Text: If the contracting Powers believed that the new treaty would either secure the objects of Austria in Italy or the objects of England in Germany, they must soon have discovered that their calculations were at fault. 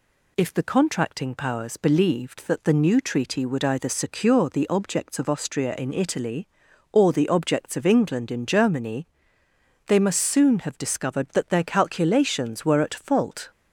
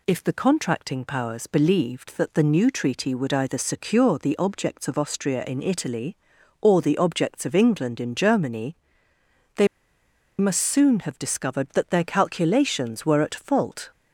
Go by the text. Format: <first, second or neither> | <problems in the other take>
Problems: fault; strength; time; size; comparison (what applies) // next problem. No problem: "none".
first | pauses between "they" and "must"; noticeable; at 9.6 s; 0.72 s long